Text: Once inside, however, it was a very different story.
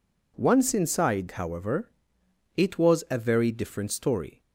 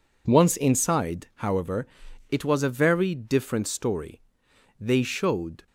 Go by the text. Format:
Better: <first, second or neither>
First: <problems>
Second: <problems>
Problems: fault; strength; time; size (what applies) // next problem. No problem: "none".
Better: first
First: none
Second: goes on to say "They showed"; noticeable; from 4.8 s on; 0.86 s long